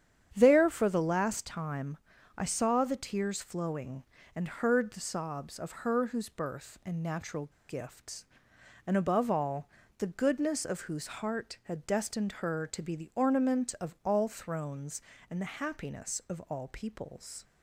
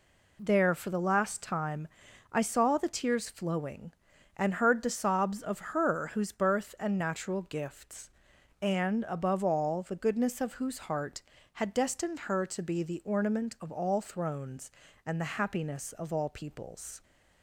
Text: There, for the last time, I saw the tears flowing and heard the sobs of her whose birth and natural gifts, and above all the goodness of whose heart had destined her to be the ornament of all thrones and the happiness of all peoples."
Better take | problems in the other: second | starts louder than the rest; strong; until 1.3 s; 9 dB // pauses between "natural" and "gifts"; slight; at 7.5 s; 0.18 s long // pauses between "all" and "the"; slight; at 9.6 s; 0.30 s long

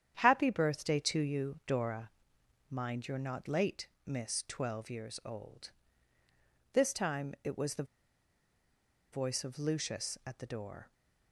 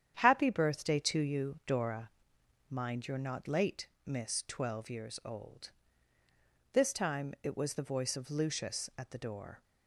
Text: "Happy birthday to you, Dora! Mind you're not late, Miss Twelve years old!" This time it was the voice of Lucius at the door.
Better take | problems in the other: second | starts louder than the rest; strong; until 1.2 s; 9 dB; strong in the second // pauses between "the" and "voice"; strong; at 7.8 s; 1.2 s long

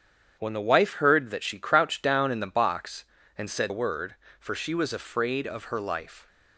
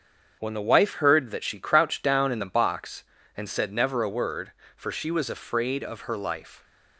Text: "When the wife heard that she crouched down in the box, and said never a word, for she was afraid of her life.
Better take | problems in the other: second | starts louder than the rest; strong; until 1.3 s; 8.5 dB; also in the second // skips "never"; at 3.7 s

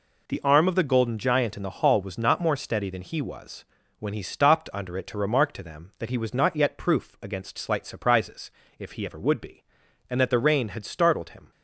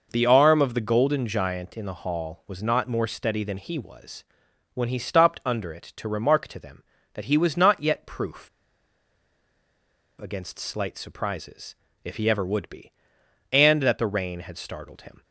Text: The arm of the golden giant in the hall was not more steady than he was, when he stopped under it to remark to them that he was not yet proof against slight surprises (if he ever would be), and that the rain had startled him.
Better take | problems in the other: first | pauses between "proof" and "against"; strong; at 8.4 s; 1.7 s long

